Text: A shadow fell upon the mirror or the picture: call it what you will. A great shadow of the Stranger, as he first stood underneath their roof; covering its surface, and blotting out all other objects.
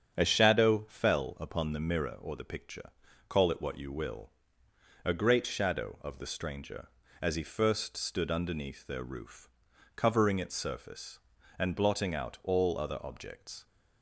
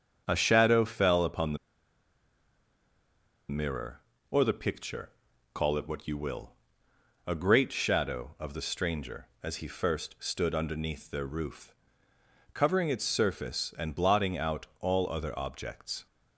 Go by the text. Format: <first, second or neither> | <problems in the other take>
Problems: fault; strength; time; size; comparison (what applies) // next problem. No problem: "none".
first | starts louder than the rest; strong; until 1.2 s; 7.5 dB; strong in the first // pauses between "the" and "mirror"; strong; at 1.5 s; 1.9 s long